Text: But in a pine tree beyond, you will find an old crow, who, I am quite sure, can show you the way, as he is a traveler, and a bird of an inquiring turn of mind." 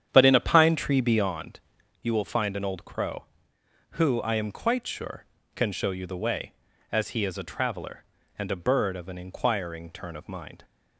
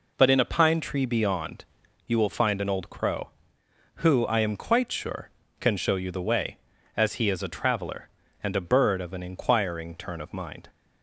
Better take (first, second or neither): second